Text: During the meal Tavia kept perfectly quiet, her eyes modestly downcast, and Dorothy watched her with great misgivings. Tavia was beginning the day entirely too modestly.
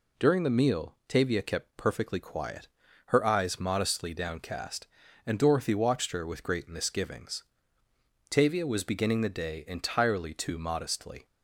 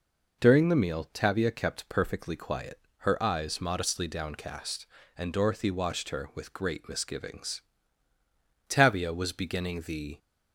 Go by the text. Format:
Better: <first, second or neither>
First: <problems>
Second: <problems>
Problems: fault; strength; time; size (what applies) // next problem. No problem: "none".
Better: first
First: none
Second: stops before "day entirely too modestly"; at 10.1 s